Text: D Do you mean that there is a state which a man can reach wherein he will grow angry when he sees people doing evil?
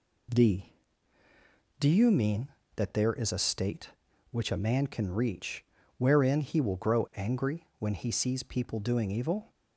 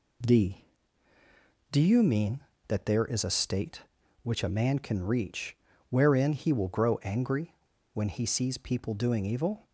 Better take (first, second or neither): first